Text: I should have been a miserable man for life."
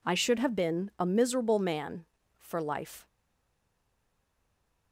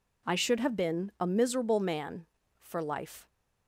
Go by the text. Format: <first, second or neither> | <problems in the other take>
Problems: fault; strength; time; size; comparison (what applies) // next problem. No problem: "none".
second | stays silent after the last word; noticeable; from 3.0 s on; 1.9 s long